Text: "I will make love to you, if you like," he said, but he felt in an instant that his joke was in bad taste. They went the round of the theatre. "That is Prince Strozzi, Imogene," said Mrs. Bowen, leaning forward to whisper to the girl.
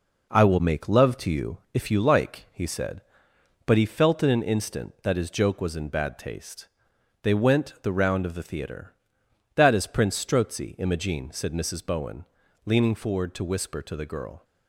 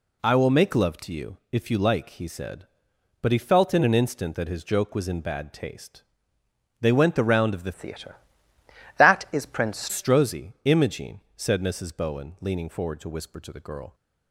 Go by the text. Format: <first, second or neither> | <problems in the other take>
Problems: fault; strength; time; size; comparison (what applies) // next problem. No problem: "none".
first | changes voice from "theatre" to "Prince"; from 7.7 to 9.8 s; 2.1 s long